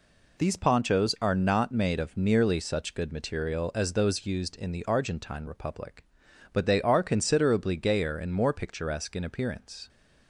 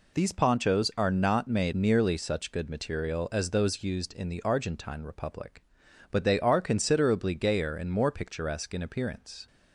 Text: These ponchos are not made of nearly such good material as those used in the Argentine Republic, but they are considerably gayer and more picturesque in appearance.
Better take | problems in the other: first | skips "of"; at 1.7 s

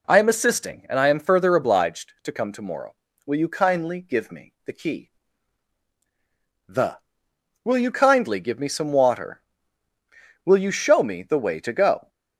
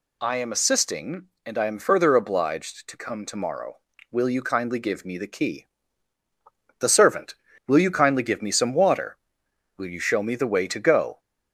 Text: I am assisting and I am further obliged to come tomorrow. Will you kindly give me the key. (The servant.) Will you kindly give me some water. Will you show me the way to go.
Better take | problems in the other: second | skips "servant"; at 7.3 s

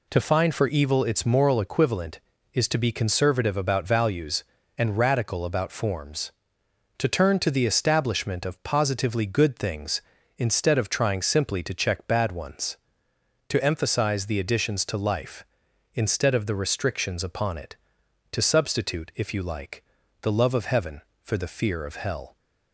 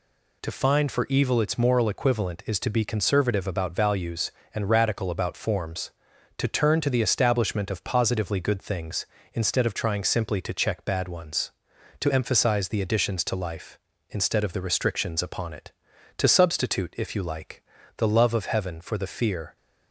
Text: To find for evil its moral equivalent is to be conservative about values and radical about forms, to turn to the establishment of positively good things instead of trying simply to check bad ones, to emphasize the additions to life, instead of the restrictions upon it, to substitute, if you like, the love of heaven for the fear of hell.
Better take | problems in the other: first | stops before "of hell"; at 19.5 s

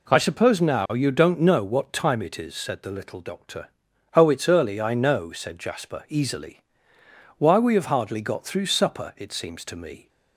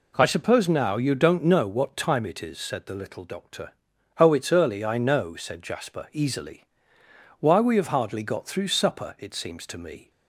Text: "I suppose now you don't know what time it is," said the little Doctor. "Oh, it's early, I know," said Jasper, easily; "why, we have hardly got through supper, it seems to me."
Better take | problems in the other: neither | none

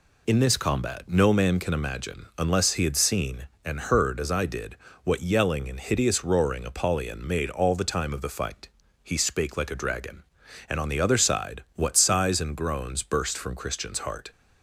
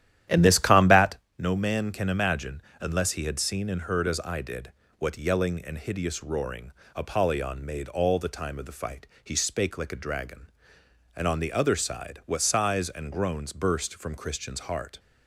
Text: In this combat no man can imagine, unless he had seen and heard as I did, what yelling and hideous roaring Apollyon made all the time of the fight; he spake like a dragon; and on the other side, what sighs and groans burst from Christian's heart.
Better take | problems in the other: first | starts louder than the rest; strong; until 1.2 s; 11.5 dB // pauses between "combat" and "no"; slight; at 1.1 s; 0.22 s long // pauses between "roaring" and "Apollyon"; slight; at 6.7 s; 0.24 s long

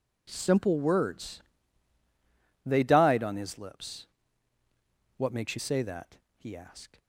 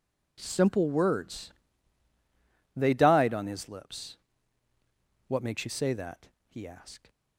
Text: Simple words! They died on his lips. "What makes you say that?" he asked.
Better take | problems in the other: neither | none

